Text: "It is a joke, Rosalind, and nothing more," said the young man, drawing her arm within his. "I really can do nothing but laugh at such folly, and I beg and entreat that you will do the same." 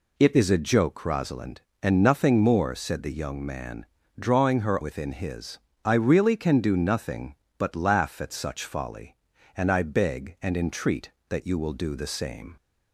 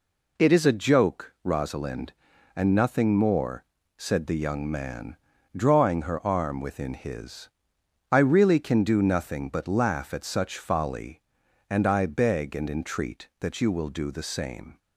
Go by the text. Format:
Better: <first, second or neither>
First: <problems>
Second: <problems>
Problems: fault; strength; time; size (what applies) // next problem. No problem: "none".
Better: second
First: skips "arm"; at 4.8 s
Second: none